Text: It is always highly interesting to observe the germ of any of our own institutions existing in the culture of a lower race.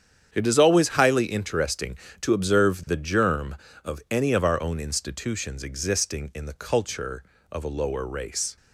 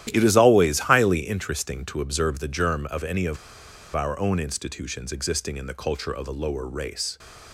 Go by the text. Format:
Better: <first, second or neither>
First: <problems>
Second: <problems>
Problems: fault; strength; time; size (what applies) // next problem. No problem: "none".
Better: first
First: starts louder than the rest; strong; until 1.3 s; 8.5 dB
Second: starts louder than the rest; strong; until 1.1 s; 12 dB // pauses between "of" and "our"; noticeable; at 3.3 s; 0.57 s long